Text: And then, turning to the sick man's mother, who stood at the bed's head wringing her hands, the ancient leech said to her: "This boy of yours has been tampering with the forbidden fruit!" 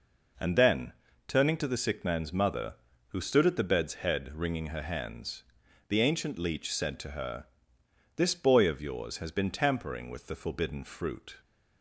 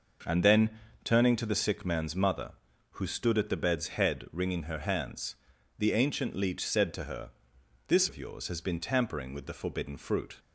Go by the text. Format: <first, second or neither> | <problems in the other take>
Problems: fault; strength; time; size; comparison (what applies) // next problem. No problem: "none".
first | skips "boy"; at 8.0 s